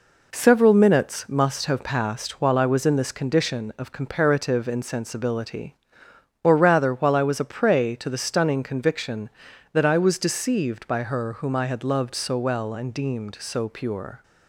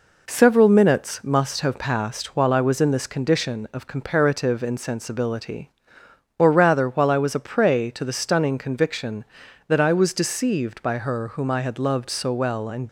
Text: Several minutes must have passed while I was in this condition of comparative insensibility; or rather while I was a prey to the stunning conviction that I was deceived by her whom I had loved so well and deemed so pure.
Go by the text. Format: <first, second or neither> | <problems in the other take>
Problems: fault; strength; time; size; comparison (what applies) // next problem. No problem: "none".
first | stops before "deemed so pure"; at 12.8 s